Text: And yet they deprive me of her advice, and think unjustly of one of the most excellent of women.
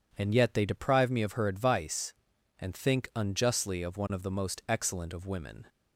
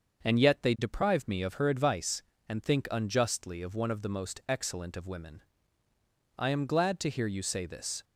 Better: first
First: none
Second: starts louder than the rest; until 1.2 s; 6.5 dB // goes on to say "I am glad to hear you say this"; from 6.3 s on; 1.6 s long

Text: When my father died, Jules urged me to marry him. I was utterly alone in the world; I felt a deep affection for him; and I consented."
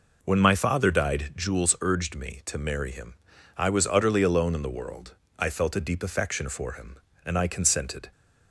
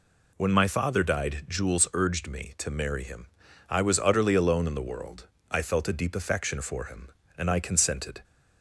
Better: second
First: starts louder than the rest; noticeable; until 1.3 s; 5 dB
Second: none

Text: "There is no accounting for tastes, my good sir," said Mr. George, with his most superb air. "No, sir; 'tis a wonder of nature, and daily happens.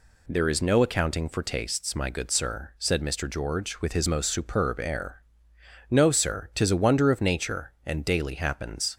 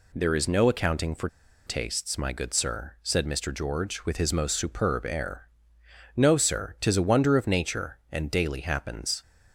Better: first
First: none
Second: pauses between "for" and "tastes"; at 1.2 s; 0.39 s long

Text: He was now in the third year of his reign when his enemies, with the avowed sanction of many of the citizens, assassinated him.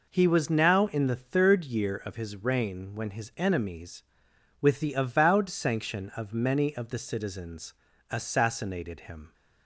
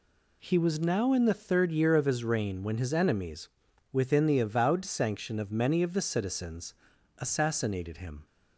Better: first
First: none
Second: says "within" for "with"; at 3.9 s

